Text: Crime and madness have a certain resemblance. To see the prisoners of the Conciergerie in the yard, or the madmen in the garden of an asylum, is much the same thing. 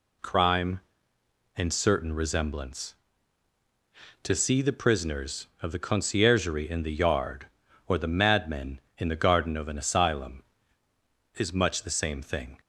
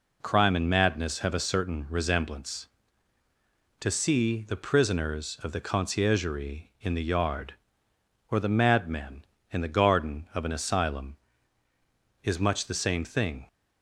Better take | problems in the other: second | skips "madness have a"; at 1.7 s

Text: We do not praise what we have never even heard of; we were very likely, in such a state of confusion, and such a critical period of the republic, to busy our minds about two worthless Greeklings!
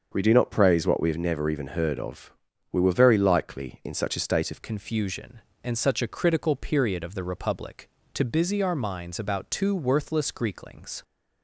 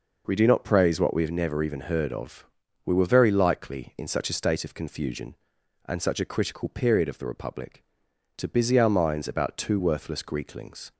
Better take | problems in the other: second | starts louder than the rest; until 1.1 s; 6.5 dB // changes voice at "confusion"; from 4.6 s on; 6.4 s long

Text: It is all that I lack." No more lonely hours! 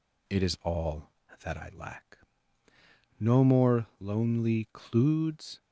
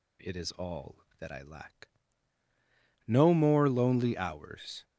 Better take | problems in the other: second | says "cludes" for "hours"; at 4.7 s

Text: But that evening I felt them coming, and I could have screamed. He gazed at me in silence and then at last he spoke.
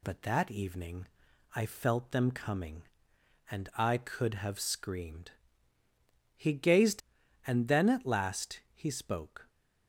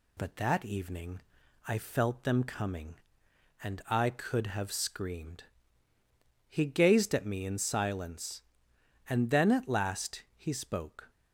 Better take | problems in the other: second | pauses between "evening" and "I"; noticeable; at 1.0 s; 0.50 s long; noticeable in the second // skips "at me in silence"; at 7.2 s

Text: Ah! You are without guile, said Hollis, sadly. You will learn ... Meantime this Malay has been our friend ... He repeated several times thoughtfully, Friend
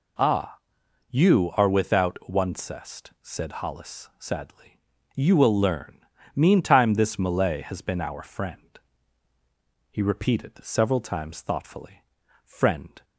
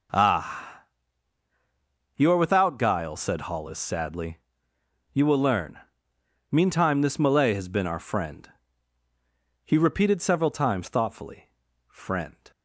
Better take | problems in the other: second | says "oncest" for "guile"; at 2.2 s

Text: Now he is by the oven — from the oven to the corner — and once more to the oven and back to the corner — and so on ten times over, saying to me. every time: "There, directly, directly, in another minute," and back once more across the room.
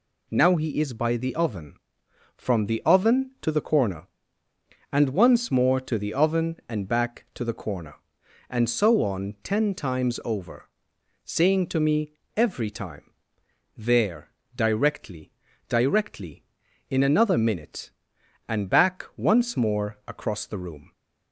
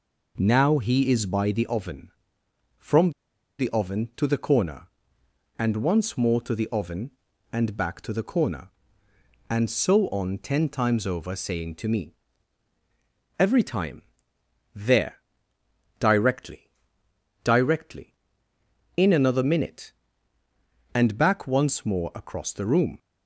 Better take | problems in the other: first | pauses between "from" and "the"; noticeable; at 3.1 s; 0.46 s long

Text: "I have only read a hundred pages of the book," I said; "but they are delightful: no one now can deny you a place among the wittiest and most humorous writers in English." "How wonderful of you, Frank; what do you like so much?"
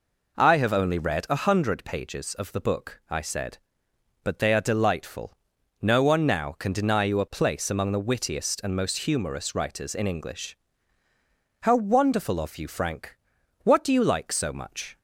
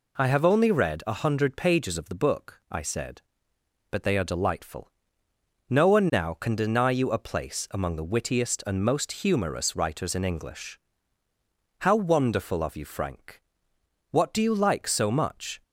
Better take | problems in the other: neither | none

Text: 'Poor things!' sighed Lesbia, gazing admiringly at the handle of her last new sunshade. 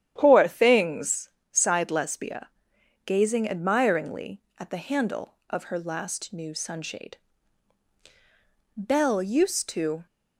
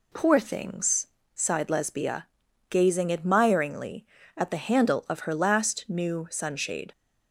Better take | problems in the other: second | starts louder than the rest; strong; until 1.1 s; 10.5 dB // goes on to say "Belle used to"; noticeable; from 8.7 s on; 1.2 s long

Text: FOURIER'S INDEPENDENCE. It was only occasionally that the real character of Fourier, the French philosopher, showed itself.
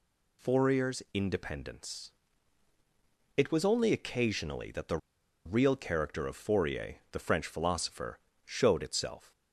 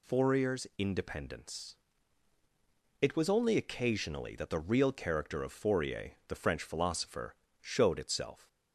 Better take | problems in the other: second | pauses between "the" and "real"; noticeable; at 4.9 s; 0.47 s long

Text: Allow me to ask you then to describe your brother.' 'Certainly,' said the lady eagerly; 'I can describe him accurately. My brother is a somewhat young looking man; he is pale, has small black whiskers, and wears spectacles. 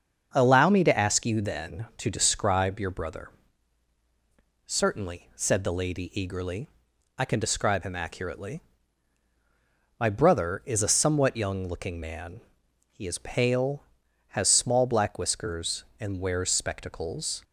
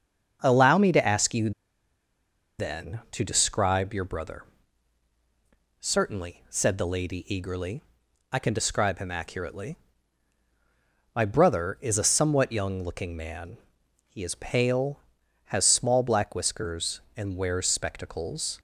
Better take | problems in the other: first | starts louder than the rest; until 1.4 s; 7 dB; also in the first // pauses between "you" and "then"; at 1.5 s; 1.0 s long

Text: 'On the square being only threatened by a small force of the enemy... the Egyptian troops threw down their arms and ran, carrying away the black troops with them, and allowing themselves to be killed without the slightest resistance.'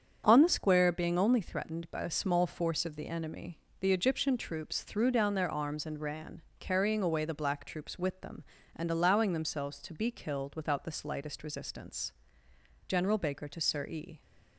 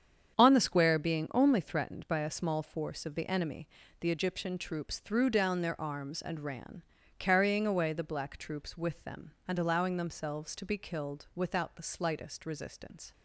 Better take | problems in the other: second | starts louder than the rest; strong; until 1.2 s; 7.5 dB; strong in the second // goes on to say "General Baker to Sir E"; from 12.8 s on; 1.3 s long

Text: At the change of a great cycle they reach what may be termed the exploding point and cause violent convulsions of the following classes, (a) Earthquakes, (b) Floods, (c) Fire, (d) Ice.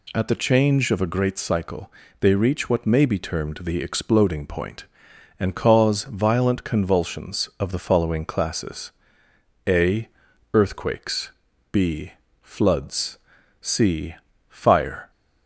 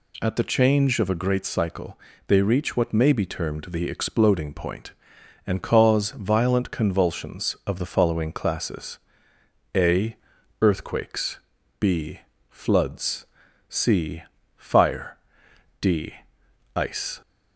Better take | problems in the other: second | pauses between "cycle" and "they"; slight; at 1.9 s; 0.30 s long; slight in the second // stops before "d Ice"; at 15.1 s

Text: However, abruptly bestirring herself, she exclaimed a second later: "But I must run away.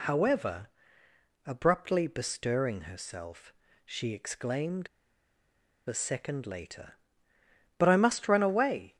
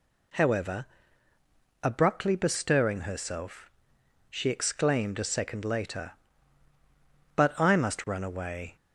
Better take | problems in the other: second | pauses between "exclaimed" and "a"; at 4.8 s; 1.0 s long

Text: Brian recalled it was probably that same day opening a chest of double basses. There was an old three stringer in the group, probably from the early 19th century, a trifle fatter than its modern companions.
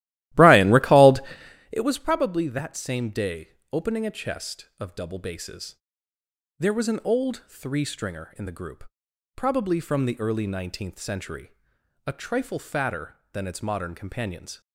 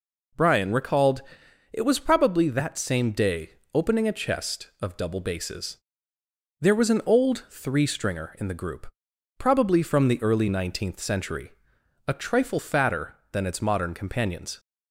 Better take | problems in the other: second | starts louder than the rest; strong; until 1.9 s; 15.5 dB // pauses between "recalled" and "it"; noticeable; at 1.2 s; 0.50 s long; noticeable in the second // pauses between "day" and "opening"; slight; at 3.4 s; 0.24 s long; slight in the second

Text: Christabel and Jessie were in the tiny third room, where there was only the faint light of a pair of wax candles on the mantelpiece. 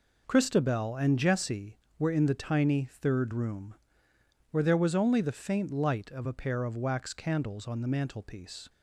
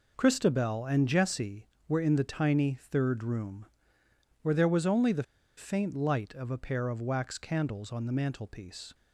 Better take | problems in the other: first | pauses between "the" and "faint"; slight; at 5.2 s; 0.32 s long

